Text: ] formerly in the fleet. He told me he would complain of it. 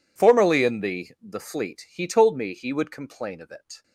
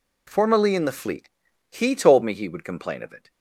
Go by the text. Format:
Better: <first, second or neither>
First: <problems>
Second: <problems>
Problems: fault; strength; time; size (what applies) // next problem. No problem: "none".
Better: second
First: says "the" twice; at 1.2 s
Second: none